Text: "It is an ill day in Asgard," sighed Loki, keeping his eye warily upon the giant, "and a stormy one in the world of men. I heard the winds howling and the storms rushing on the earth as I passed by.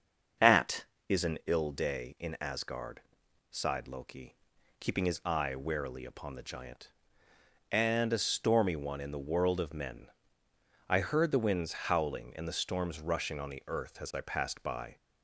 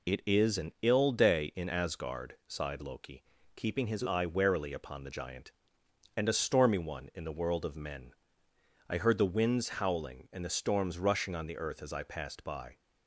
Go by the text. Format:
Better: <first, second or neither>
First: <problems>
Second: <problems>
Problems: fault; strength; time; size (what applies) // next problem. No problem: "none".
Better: second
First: starts louder than the rest; until 1.7 s; 6.5 dB // says "At" for "It"; at 0.3 s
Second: none